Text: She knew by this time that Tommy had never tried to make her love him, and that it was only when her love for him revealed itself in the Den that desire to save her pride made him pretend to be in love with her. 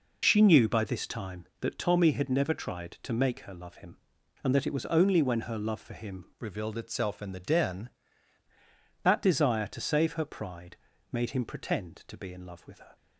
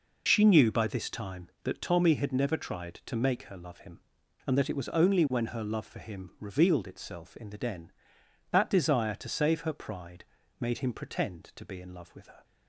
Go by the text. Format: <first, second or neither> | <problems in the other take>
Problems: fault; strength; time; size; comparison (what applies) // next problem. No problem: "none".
second | changes voice from "revealed" to "Den"; from 6.3 to 7.8 s; 1.5 s long // pauses between "pride" and "made"; slight; at 10.7 s; 0.34 s long; slight in the second